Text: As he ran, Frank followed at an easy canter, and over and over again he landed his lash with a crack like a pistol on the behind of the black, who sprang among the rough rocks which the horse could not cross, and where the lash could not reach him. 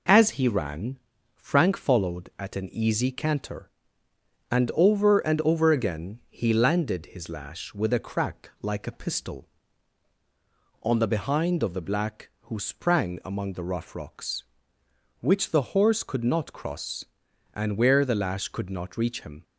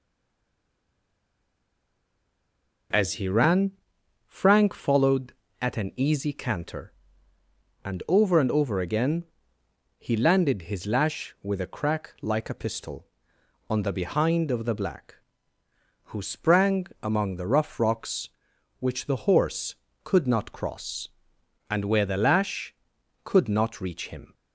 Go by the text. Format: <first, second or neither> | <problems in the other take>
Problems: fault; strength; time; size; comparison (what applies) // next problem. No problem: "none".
first | stays silent before the first word; strong; until 2.9 s; 2.9 s long // pauses between "again" and "he"; noticeable; at 9.2 s; 0.74 s long // pauses between "sprang" and "among"; slight; at 16.8 s; 0.16 s long